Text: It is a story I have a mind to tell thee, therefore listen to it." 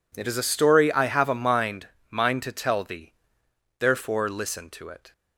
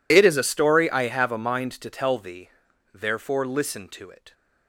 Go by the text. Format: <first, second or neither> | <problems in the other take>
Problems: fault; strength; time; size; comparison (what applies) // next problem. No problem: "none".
second | says "mind" twice; at 2.1 s